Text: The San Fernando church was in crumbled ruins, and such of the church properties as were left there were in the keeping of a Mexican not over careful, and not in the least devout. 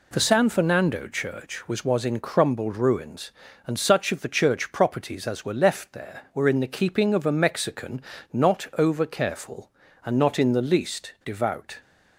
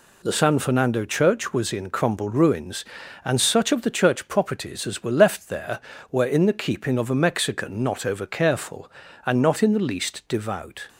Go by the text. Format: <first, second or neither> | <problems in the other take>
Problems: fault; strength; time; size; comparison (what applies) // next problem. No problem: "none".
second | says "was" twice; at 1.8 s // pauses between "Mexican" and "not"; slight; at 8.0 s; 0.28 s long